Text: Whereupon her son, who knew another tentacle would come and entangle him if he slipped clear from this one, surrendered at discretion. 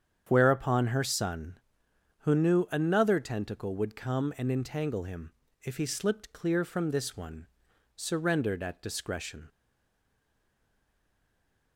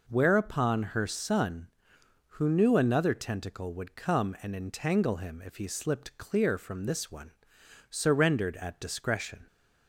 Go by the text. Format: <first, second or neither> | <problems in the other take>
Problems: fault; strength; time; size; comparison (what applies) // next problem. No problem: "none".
second | starts louder than the rest; strong; until 1.2 s; 8 dB // pauses between "him" and "if"; slight; at 5.3 s; 0.30 s long // stays silent after the last word; from 9.4 s on; 2.3 s long